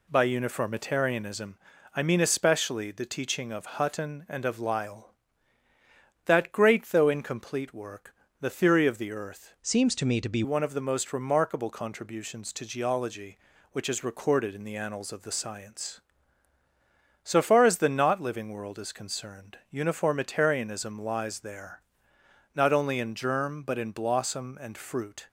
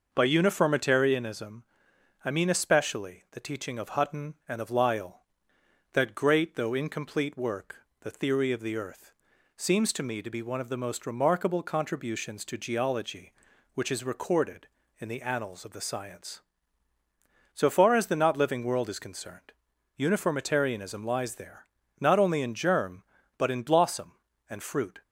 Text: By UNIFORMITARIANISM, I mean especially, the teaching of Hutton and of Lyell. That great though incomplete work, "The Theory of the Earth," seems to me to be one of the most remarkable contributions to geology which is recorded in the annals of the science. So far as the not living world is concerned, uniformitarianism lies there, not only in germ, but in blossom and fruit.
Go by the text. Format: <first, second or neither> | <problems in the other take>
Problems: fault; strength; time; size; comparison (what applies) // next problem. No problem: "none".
second | changes voice from "seems" to "be"; from 9.6 to 10.4 s; 0.8 s long